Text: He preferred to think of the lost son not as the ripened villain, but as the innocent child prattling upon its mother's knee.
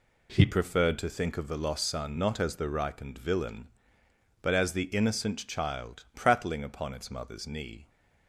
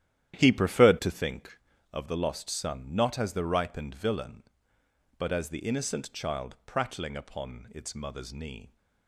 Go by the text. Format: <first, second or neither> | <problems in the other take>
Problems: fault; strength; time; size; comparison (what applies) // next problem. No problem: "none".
first | starts louder than the rest; strong; until 1.5 s; 11.5 dB